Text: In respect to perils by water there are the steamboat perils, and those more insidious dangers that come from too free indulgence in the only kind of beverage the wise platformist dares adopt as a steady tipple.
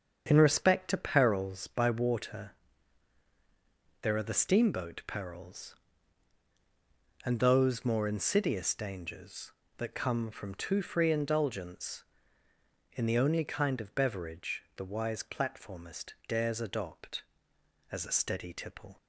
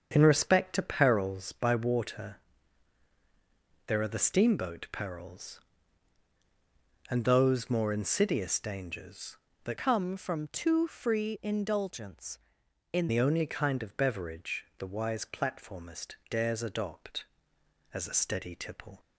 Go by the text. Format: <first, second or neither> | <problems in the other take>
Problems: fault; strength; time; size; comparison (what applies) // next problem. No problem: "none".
first | starts louder than the rest; strong; until 1.1 s; 7 dB; strong in the first // pauses between "water" and "there"; strong; at 2.3 s; 1.5 s long; strong in the first // changes voice from "come" to "in"; from 9.7 to 13.0 s; 3.3 s long